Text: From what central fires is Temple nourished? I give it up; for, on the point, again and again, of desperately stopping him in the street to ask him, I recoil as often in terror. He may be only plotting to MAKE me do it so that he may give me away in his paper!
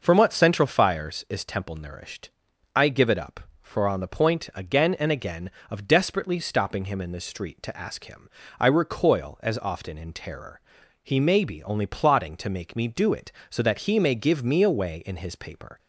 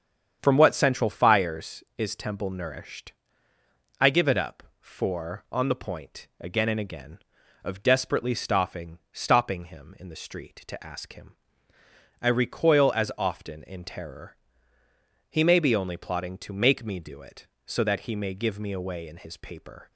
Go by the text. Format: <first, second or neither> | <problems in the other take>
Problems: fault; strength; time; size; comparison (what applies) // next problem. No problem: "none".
first | starts louder than the rest; strong; until 1.4 s; 8 dB // says "stopping" twice; at 9.1 s